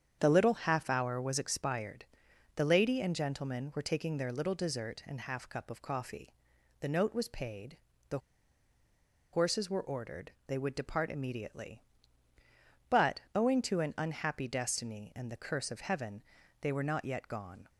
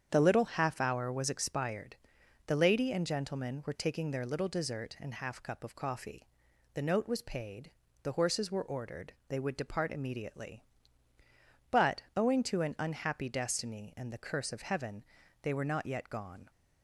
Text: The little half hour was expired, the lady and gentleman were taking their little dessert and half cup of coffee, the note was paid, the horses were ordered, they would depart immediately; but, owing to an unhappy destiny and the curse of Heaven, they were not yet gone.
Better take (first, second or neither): second